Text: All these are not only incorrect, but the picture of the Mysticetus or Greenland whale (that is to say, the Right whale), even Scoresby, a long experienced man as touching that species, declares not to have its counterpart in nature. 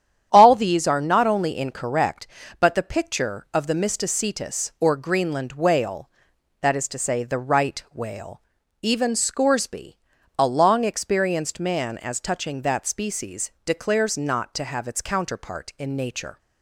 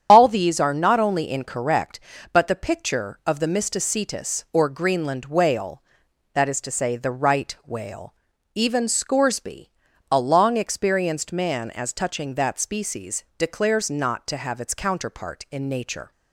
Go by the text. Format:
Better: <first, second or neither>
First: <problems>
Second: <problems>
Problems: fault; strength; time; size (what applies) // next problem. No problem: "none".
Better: first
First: starts louder than the rest; strong; until 1.3 s; 9.5 dB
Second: loses the start of "All"; at 0.0 s; 55 ms // starts louder than the rest; strong; until 1.1 s; 9 dB